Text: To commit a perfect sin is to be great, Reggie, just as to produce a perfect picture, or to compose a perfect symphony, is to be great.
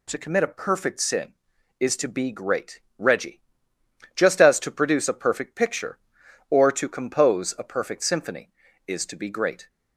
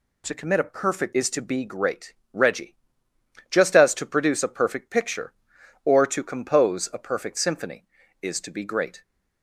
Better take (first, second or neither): first